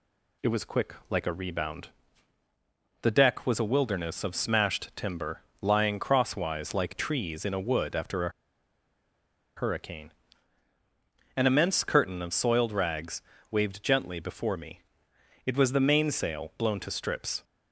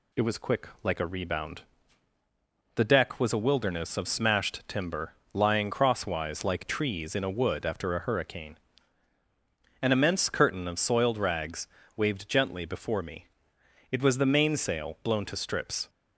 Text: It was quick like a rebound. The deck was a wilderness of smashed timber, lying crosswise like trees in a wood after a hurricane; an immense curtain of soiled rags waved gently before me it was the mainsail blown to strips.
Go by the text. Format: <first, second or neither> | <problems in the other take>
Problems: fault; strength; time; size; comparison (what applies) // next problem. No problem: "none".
second | pauses between "a" and "hurricane"; strong; at 8.2 s; 1.2 s long // pauses between "rags" and "waved"; slight; at 13.2 s; 0.28 s long; slight in the second // pauses between "me" and "it"; noticeable; at 14.8 s; 0.64 s long; noticeable in the second